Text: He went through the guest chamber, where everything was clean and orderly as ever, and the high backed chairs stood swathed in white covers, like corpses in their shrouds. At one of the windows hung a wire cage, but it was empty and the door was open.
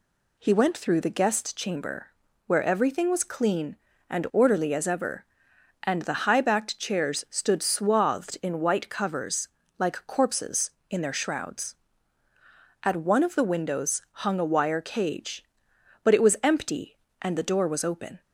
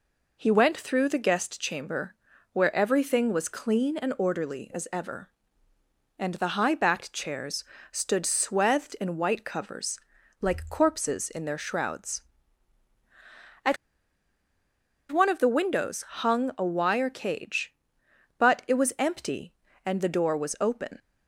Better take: first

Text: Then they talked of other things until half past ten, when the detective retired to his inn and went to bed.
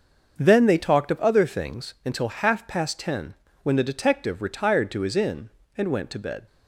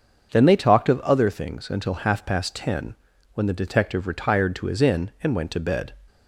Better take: neither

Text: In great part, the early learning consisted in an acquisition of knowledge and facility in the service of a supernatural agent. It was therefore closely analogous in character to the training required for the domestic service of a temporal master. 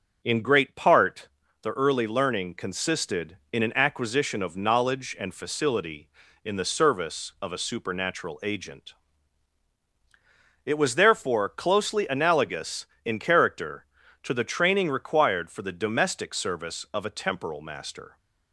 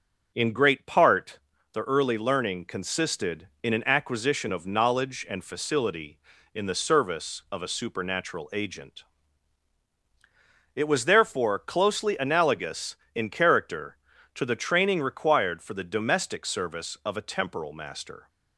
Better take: neither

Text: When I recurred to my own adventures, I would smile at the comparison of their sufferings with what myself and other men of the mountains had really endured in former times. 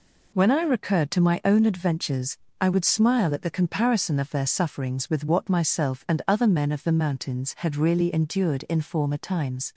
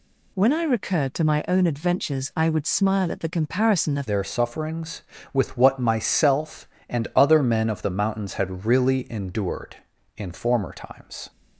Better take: first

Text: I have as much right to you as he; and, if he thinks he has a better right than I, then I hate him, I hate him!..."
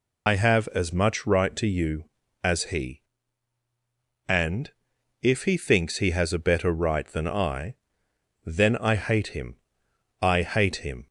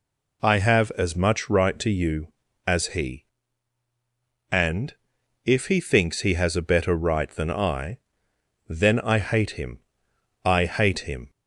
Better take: second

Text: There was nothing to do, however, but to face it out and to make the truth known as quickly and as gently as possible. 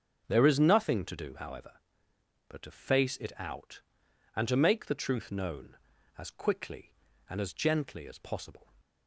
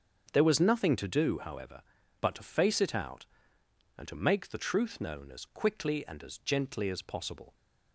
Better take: second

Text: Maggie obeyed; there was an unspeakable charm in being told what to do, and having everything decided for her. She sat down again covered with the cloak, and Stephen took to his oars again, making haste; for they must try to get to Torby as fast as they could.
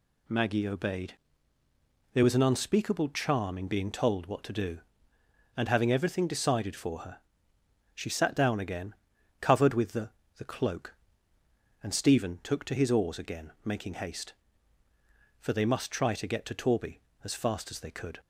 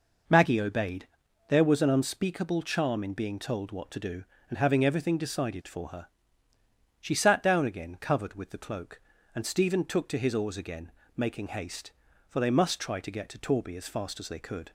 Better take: second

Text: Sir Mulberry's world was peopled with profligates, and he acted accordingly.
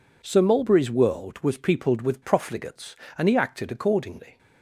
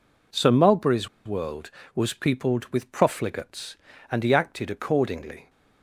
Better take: first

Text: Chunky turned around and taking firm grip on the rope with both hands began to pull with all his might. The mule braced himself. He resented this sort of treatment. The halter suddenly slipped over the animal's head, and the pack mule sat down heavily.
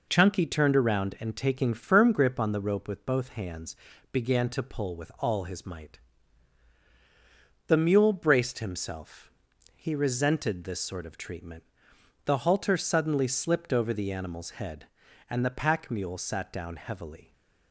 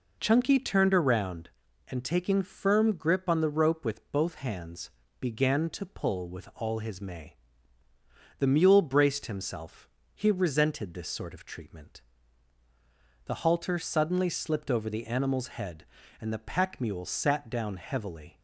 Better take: first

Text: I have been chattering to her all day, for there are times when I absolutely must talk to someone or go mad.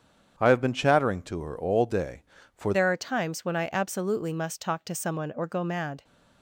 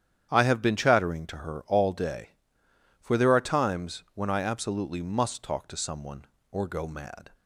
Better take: second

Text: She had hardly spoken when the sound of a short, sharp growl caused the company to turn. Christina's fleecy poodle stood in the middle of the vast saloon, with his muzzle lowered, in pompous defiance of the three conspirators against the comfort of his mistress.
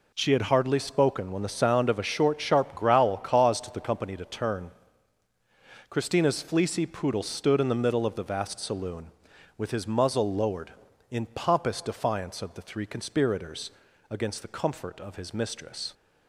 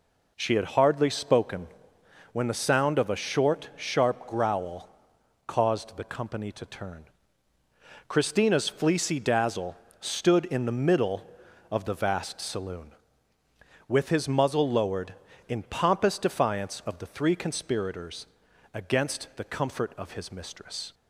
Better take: first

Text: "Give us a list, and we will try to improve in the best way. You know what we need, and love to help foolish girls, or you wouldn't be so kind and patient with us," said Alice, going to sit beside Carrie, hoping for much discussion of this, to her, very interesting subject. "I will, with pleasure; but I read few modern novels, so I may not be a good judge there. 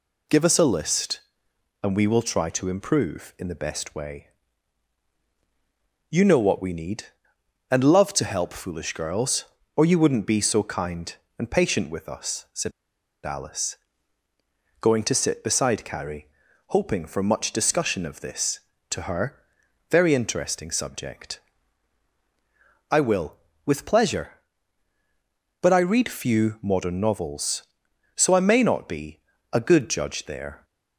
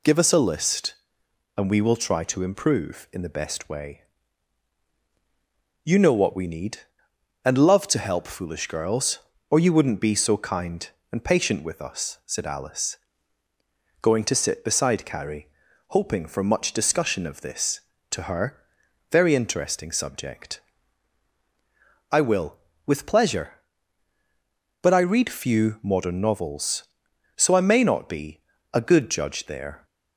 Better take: second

